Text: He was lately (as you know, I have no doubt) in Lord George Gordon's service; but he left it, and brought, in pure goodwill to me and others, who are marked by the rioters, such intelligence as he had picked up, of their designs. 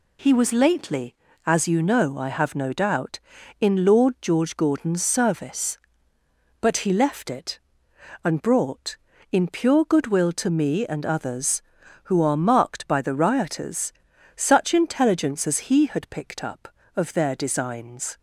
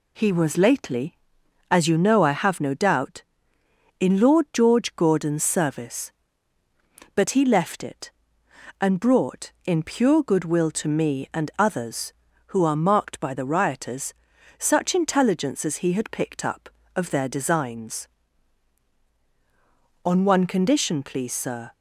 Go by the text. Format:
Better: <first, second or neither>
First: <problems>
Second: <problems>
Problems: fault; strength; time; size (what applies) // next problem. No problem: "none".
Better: first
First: none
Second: goes on to say "On one condition please sir"; strong; from 20.0 s on; 1.7 s long